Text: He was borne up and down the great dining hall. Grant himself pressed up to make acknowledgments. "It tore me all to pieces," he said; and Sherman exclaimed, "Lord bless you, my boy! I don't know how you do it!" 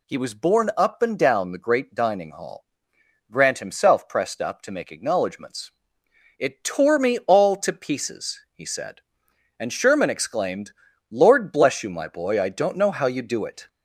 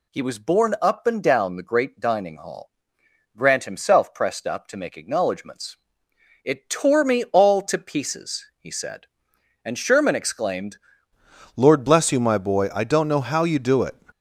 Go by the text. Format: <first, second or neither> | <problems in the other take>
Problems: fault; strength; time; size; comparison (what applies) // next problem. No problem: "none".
first | changes voice at "Lord"; from 11.5 s on; 2.4 s long